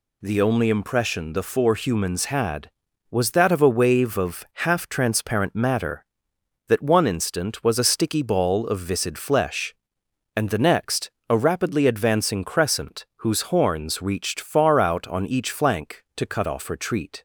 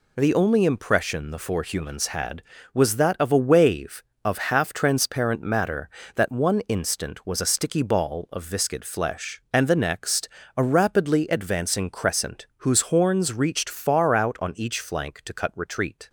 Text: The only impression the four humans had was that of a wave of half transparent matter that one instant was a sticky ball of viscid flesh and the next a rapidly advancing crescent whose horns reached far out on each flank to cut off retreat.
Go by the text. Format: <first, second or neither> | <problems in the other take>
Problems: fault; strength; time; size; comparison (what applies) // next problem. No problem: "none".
first | pauses between "next" and "a"; slight; at 10.2 s; 0.30 s long; slight in the first // skips "off"; at 15.5 s